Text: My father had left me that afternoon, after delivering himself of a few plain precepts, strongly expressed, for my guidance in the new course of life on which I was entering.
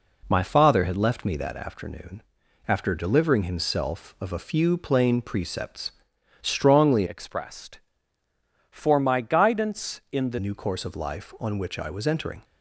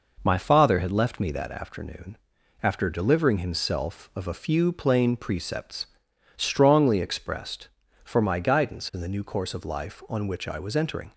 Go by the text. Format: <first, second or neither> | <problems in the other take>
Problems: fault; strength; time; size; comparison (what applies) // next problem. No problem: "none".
second | changes voice from "expressed" to "the"; from 7.0 to 10.3 s; 3.3 s long